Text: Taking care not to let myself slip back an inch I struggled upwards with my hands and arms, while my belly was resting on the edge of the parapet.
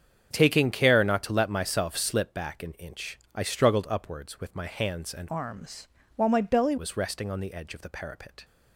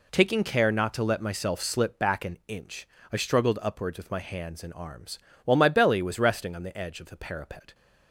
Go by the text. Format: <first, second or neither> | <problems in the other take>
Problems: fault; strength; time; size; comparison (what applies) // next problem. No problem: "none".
second | starts louder than the rest; strong; until 1.3 s; 7.5 dB // pauses between "inch" and "I"; slight; at 3.1 s; 0.18 s long; slight in the second // changes voice from "arms" to "belly"; from 5.2 to 6.7 s; 1.5 s long